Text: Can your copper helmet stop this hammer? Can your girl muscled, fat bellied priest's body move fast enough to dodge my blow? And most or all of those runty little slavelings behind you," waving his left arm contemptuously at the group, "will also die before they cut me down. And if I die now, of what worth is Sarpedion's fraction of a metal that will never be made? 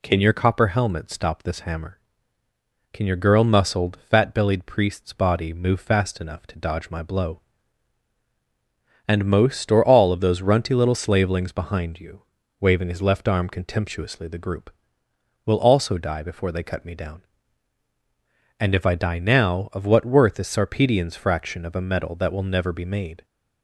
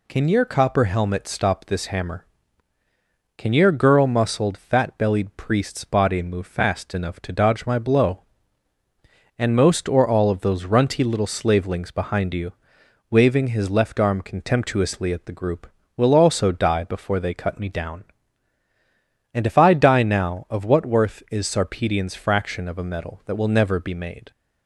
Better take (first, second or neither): second